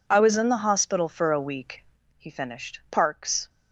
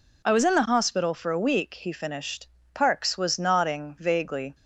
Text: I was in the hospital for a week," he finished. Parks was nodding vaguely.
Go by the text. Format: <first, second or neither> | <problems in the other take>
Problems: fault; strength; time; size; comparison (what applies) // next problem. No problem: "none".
second | stops before "was nodding vaguely"; at 3.4 s